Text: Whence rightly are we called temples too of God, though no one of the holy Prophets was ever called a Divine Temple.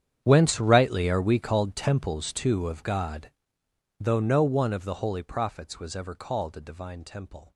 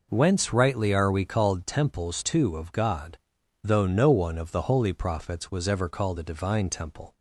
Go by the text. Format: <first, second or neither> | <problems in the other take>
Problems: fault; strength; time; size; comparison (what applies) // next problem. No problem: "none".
second | gets quieter; strong; throughout; 19.5 dB